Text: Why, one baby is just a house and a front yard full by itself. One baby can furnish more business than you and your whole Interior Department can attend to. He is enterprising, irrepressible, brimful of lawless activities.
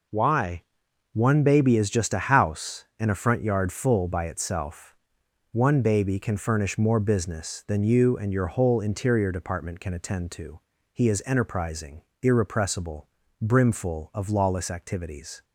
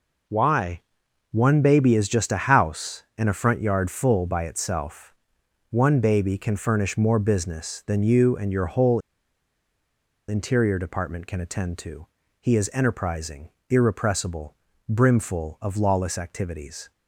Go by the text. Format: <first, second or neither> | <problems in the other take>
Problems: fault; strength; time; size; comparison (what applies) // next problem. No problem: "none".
first | pauses between "whole" and "Interior"; strong; at 8.9 s; 1.2 s long